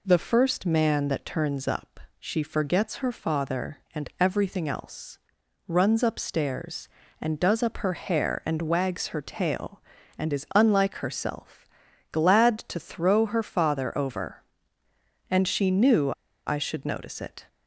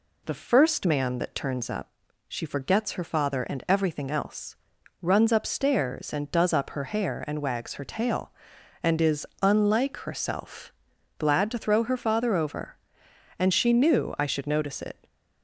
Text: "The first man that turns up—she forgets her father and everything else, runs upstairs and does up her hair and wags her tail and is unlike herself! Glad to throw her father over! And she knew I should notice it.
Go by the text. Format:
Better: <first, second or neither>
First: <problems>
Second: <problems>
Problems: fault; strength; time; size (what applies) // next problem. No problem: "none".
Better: second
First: pauses between "knew" and "I"; slight; at 16.1 s; 0.35 s long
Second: none